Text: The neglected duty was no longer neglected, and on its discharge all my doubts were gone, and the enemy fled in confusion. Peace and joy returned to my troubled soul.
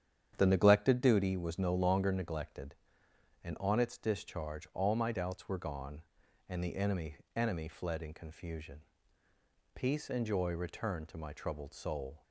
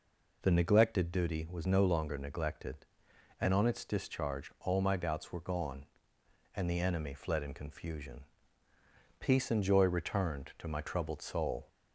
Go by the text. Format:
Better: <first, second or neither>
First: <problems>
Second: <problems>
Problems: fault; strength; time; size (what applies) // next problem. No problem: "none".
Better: second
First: starts louder than the rest; strong; until 1.3 s; 9.5 dB // says "enemy" twice; at 7.3 s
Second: none